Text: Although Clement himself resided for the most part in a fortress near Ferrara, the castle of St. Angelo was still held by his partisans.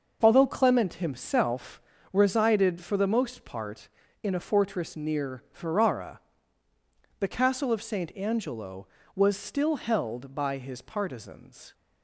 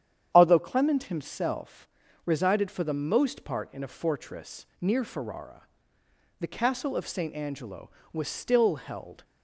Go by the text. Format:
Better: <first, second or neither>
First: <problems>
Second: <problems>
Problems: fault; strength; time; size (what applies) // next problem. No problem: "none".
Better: first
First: pauses between "himself" and "resided"; slight; at 1.8 s; 0.32 s long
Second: starts louder than the rest; strong; until 1.3 s; 9 dB // pauses between "himself" and "resided"; at 1.8 s; 0.38 s long // pauses between "fortress" and "near"; slight; at 4.6 s; 0.16 s long // stops before "by his partisans"; at 9.2 s